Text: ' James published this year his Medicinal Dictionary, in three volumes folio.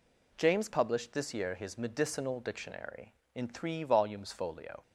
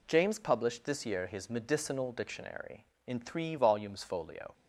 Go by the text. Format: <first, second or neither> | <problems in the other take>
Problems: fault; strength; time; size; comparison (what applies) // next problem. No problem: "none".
neither | none